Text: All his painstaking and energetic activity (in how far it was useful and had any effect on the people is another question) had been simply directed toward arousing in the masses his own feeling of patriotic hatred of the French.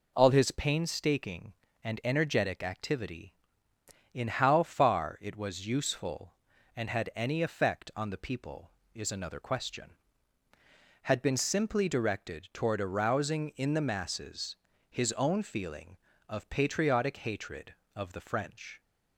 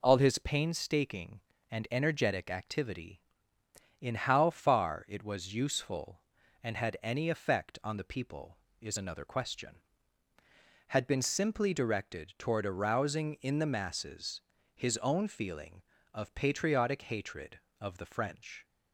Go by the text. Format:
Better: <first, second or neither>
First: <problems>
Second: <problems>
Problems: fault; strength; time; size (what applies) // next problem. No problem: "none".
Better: neither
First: pauses between "masses" and "his"; slight; at 14.5 s; 0.36 s long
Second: pauses between "masses" and "his"; slight; at 14.4 s; 0.36 s long